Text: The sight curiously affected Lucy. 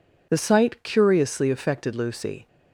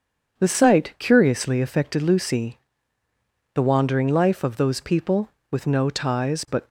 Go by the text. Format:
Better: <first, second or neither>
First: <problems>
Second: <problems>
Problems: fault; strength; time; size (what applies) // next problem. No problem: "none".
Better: first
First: none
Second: starts louder than the rest; until 1.4 s; 7 dB // goes on to say "The wandering life of those people with no ties but"; strong; from 3.5 s on; 3.1 s long